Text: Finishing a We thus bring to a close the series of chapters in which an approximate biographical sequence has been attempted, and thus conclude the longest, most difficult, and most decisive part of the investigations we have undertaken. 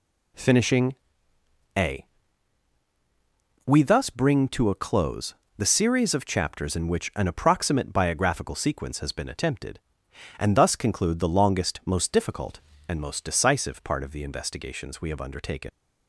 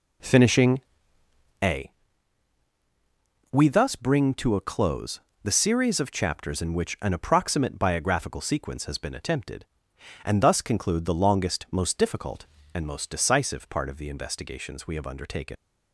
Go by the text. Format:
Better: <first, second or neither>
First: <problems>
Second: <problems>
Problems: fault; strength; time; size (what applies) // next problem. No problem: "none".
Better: first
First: pauses between "Finishing" and "a"; noticeable; at 0.9 s; 0.82 s long // pauses between "a" and "We"; strong; at 2.0 s; 1.6 s long // pauses between "close" and "the"; slight; at 5.3 s; 0.24 s long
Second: starts louder than the rest; until 1.8 s; 3.5 dB // pauses between "Finishing" and "a"; noticeable; at 0.8 s; 0.82 s long // pauses between "a" and "We"; strong; at 1.9 s; 1.6 s long // pauses between "close" and "the"; slight; at 5.1 s; 0.24 s long